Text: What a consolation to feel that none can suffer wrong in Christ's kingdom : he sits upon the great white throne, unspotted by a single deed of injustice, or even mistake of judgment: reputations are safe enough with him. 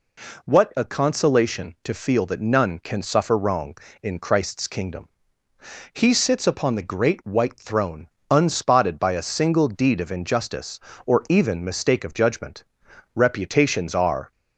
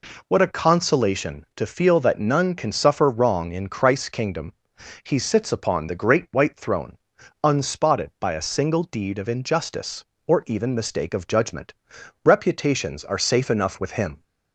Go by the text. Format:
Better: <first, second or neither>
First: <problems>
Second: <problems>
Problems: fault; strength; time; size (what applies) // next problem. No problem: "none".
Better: second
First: stops before "safe enough with him"; at 14.3 s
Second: none